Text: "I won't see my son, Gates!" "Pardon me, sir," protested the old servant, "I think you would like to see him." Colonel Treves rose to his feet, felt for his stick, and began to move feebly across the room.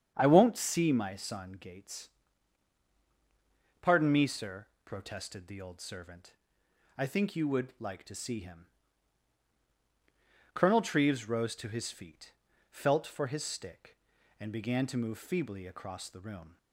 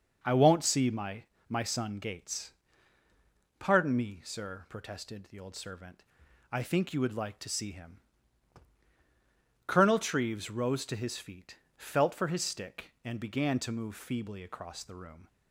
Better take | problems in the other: first | starts louder than the rest; until 1.2 s; 6 dB; strong in the first // says "my" twice; at 1.4 s

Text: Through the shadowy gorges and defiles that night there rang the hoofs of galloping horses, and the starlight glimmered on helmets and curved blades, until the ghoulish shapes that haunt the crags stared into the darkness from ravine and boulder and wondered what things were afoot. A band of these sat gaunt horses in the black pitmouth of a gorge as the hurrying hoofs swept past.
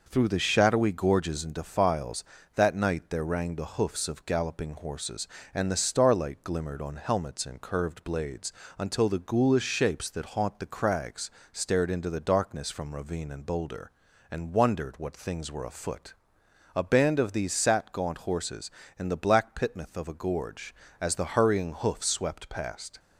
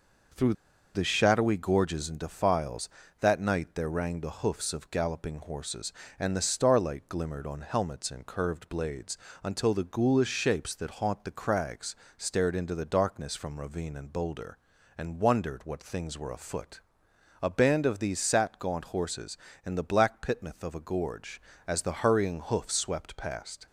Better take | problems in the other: first | pauses between "Through" and "the"; at 0.5 s; 0.40 s long // pauses between "crags" and "stared"; slight; at 11.9 s; 0.22 s long; slight in the first

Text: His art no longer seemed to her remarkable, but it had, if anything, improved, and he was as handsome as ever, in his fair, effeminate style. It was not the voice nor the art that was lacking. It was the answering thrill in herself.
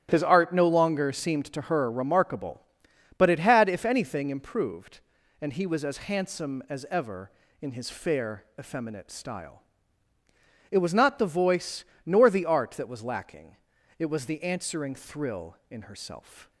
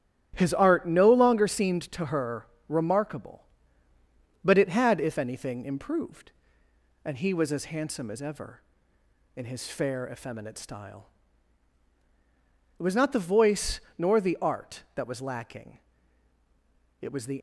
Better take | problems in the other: first | starts louder than the rest; strong; until 1.3 s; 11.5 dB; strong in the first // pauses between "her" and "remarkable"; slight; at 2.4 s; 0.20 s long // pauses between "voice" and "nor"; slight; at 13.7 s; 0.18 s long; slight in the first // stops before "answering thrill in herself"; at 17.3 s

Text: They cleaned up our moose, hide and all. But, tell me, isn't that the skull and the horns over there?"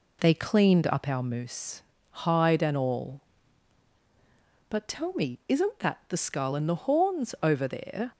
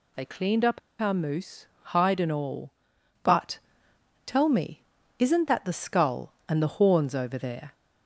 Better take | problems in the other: first | pauses between "up" and "our"; slight; at 0.7 s; 0.21 s long

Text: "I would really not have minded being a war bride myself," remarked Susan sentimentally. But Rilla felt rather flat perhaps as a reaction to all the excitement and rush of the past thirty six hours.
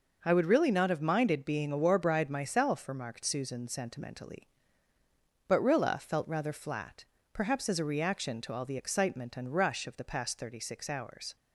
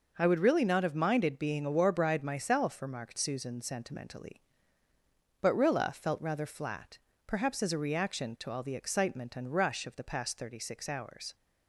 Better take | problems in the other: neither | pauses between "flat" and "perhaps"; slight; the same in both

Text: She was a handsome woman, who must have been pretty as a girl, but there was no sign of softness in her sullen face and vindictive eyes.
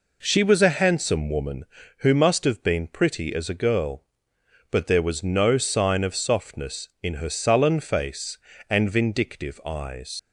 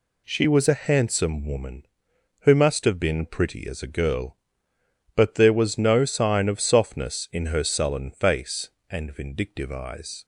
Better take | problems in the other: second | leaves "eyes" unfinished; at 10.1 s; 75 ms

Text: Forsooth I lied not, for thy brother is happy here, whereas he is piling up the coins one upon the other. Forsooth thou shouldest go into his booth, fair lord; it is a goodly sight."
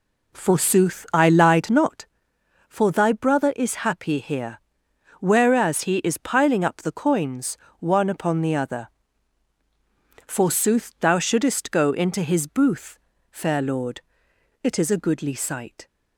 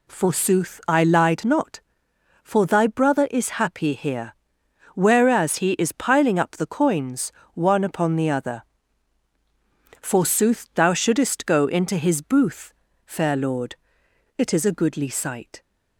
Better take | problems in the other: second | starts louder than the rest; slight; until 2.0 s; 3 dB // pauses between "coins" and "one"; slight; at 7.5 s; 0.24 s long; slight in the second

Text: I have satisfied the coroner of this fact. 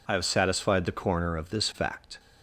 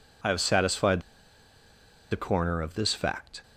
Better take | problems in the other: first | pauses between "satisfied" and "the"; at 1.0 s; 1.0 s long

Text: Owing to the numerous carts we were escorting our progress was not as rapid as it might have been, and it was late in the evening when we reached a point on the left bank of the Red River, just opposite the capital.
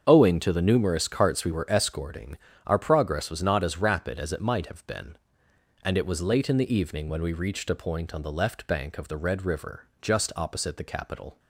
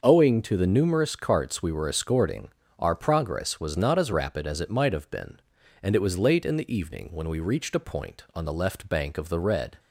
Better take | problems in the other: first | starts louder than the rest; until 1.0 s; 6.5 dB; strong in the first // pauses between "escorting" and "our"; slight; at 2.5 s; 0.28 s long; slight in the first // stops before "River just opposite the capital"; at 9.7 s

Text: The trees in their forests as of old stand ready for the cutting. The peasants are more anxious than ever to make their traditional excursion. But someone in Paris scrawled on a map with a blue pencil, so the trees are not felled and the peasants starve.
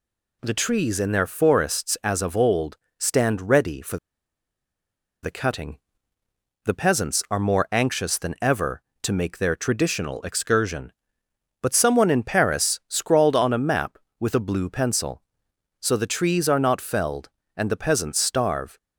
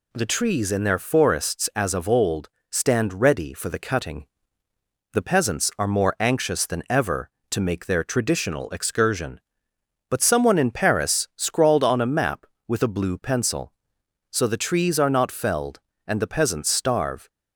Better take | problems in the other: second | pauses between "old" and "stand"; slight; at 2.7 s; 0.20 s long; slight in the second // pauses between "for" and "the"; strong; at 3.9 s; 1.2 s long

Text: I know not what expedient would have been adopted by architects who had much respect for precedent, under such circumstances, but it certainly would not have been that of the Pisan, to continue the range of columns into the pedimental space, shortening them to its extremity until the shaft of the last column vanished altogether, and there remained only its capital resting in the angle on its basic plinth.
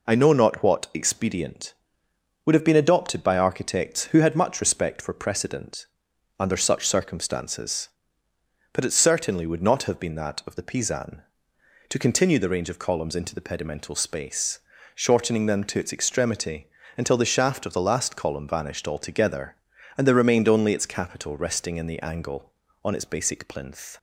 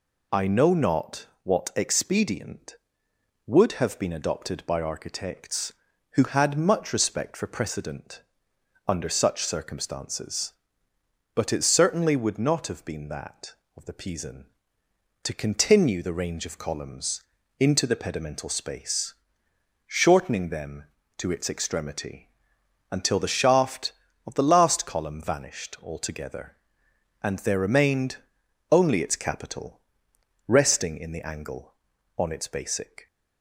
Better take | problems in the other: first | pauses between "not" and "what"; slight; at 1.2 s; 0.16 s long // pauses between "columns" and "into"; slight; at 17.2 s; 0.36 s long // pauses between "extremity" and "until"; noticeable; at 22.2 s; 0.62 s long; slight in the first // pauses between "remained" and "only"; noticeable; at 28.1 s; 0.54 s long // pauses between "capital" and "resting"; noticeable; at 29.8 s; 0.66 s long // stops before "plinth"; at 33.0 s

